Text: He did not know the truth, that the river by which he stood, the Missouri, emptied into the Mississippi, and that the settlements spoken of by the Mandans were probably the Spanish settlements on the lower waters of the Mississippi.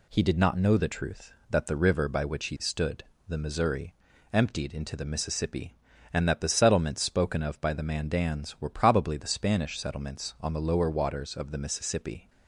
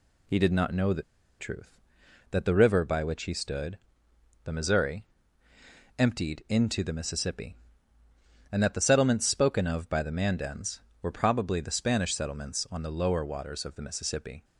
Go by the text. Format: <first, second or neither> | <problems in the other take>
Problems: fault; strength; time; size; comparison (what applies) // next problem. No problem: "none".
first | pauses between "the" and "truth"; at 1.0 s; 0.36 s long